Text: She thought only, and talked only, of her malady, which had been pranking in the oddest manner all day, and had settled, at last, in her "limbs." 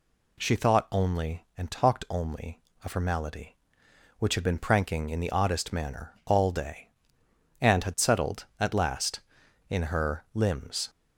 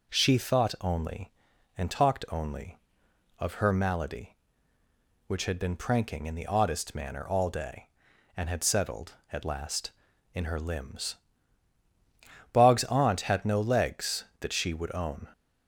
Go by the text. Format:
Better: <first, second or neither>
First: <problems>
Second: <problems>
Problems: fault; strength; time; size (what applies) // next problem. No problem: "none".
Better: first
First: none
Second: goes on to say "Bog's aunt had no legs that she would own"; strong; from 12.5 s on; 2.7 s long